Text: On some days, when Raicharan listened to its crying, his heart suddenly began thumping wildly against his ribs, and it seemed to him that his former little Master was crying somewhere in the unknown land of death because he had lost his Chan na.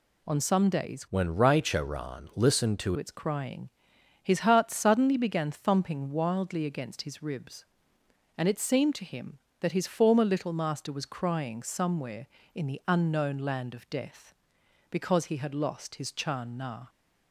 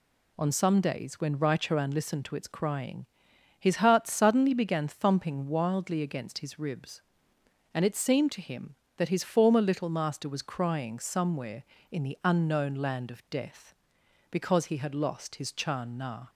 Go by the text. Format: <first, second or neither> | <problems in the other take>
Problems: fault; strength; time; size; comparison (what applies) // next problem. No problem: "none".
second | changes voice from "when" to "to"; from 1.0 to 2.9 s; 1.9 s long